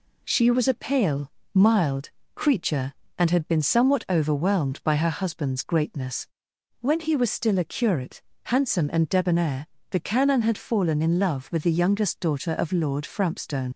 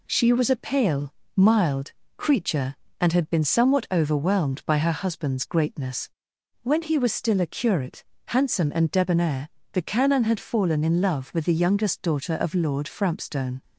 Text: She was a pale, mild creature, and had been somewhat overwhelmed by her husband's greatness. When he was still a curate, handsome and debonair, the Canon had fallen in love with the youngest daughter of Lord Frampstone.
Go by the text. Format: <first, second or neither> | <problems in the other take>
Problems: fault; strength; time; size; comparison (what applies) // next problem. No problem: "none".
second | pauses between "mild" and "creature"; slight; at 2.0 s; 0.24 s long; slight in the second // leaves "Frampstone" unfinished; at 13.7 s; 70 ms